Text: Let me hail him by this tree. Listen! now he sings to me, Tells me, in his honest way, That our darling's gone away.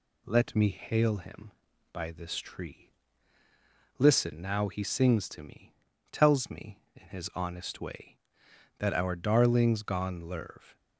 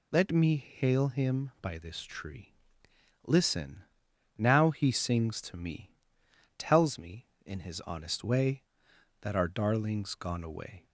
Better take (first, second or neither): second